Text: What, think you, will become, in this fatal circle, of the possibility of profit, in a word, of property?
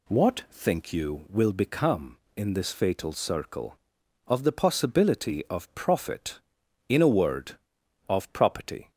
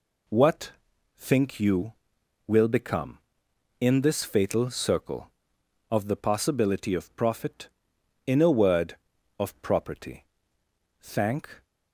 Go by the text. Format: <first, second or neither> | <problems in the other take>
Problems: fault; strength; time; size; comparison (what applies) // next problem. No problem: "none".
first | goes on to say "Thank"; noticeable; from 10.9 s on; 0.66 s long